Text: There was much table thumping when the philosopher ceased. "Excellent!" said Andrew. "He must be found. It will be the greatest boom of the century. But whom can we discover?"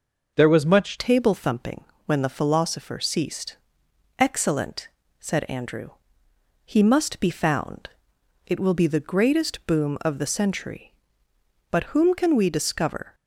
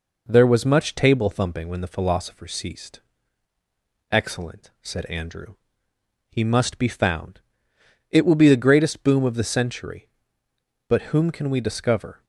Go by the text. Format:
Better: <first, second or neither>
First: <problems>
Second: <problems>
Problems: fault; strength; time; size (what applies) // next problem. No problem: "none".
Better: second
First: changes voice at "table"; from 0.9 s on; 12.2 s long // pauses between "thumping" and "when"; slight; at 1.8 s; 0.22 s long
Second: none